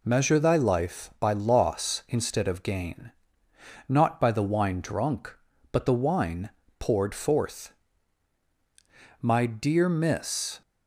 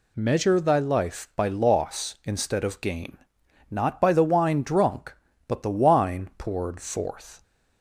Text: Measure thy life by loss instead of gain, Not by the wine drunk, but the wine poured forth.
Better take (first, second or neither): second